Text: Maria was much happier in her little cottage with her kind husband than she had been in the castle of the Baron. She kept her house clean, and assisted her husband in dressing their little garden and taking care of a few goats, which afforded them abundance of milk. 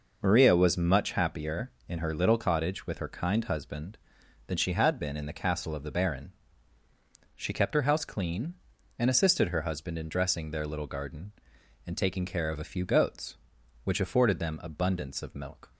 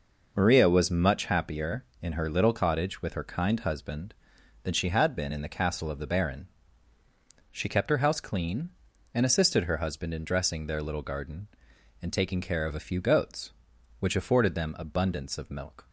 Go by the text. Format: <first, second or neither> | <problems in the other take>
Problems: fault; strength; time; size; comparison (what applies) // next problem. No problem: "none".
neither | none